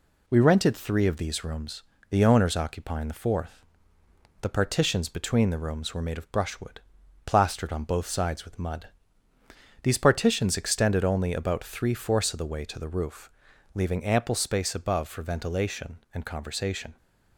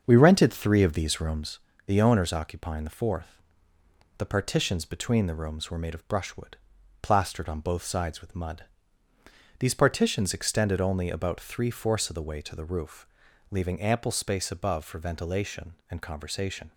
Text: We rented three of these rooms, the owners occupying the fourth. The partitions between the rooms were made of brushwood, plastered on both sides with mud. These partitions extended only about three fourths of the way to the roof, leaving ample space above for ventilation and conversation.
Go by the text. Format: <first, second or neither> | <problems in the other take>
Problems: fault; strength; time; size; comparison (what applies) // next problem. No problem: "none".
first | starts louder than the rest; until 1.7 s; 7 dB